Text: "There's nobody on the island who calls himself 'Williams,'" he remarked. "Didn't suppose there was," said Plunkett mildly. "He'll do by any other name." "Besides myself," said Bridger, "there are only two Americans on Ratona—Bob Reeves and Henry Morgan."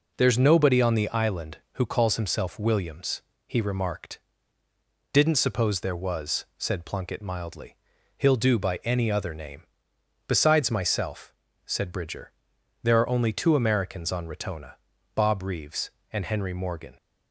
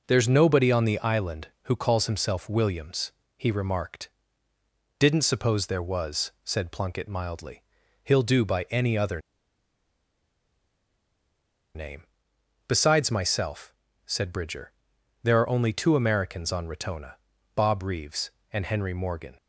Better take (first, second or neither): first